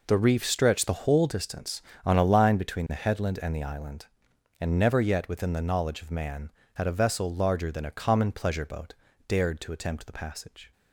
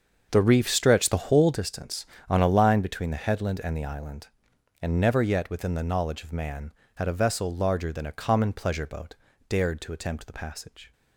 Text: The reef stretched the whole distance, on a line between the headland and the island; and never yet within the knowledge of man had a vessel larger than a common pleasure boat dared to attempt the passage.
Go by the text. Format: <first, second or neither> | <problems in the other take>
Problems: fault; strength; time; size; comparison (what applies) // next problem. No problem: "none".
first | starts louder than the rest; until 1.7 s; 6.5 dB // pauses between "boat" and "dared"; slight; at 9.1 s; 0.34 s long; slight in the first